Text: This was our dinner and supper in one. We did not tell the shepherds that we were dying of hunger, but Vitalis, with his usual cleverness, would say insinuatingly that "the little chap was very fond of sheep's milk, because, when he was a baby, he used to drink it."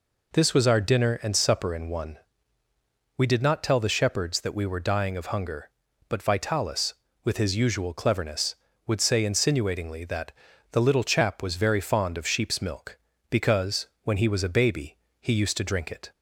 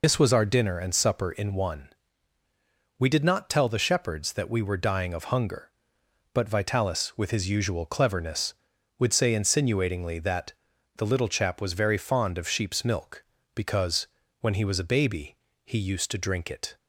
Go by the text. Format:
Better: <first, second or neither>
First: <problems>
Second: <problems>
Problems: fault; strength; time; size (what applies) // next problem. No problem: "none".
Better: first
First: pauses between "that" and "the"; at 10.3 s; 0.38 s long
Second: loses the start of "This"; at 0.0 s; 55 ms // pauses between "that" and "the"; at 10.5 s; 0.44 s long